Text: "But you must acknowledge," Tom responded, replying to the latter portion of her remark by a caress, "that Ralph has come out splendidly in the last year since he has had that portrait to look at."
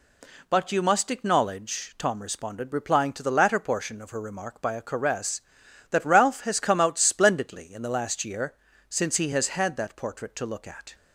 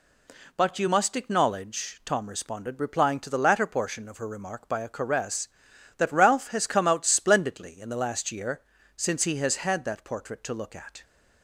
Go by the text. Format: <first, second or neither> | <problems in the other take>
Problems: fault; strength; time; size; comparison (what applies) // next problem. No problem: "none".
neither | pauses between "year" and "since"; slight; the same in both